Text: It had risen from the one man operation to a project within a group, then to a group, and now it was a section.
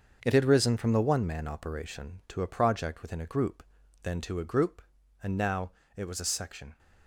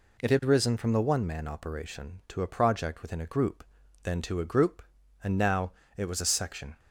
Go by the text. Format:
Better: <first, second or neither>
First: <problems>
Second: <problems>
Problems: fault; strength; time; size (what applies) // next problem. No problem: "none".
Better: second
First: gets quieter; strong; throughout; 9.5 dB // pauses between "now" and "it"; slight; at 5.7 s; 0.26 s long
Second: pauses between "now" and "it"; slight; at 5.7 s; 0.26 s long